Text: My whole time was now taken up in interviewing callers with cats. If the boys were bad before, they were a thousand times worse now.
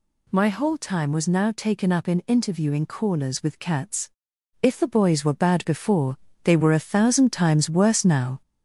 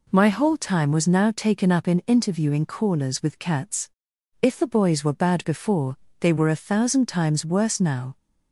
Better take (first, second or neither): second